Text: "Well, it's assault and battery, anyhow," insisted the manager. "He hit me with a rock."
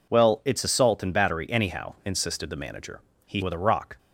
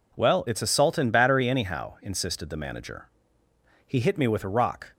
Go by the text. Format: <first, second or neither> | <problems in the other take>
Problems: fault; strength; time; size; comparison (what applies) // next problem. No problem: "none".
second | skips "hit me"; at 3.4 s